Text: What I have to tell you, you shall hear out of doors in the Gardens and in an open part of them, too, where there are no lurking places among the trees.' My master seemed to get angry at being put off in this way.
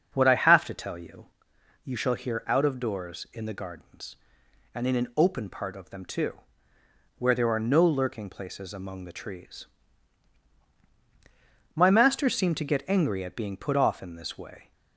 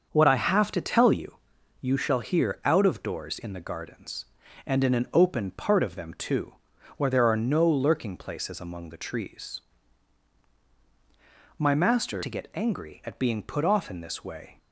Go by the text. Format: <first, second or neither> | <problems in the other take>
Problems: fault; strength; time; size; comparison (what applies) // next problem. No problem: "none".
first | starts louder than the rest; until 1.1 s; 6.5 dB; also in the first // skips "seemed"; at 12.2 s